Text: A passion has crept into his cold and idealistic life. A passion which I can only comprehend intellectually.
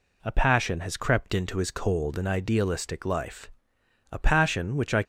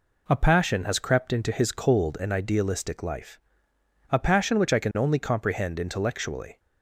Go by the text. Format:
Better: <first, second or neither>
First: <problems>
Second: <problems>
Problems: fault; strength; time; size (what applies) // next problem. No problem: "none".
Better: second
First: stops before "can only comprehend intellectually"; at 5.0 s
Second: none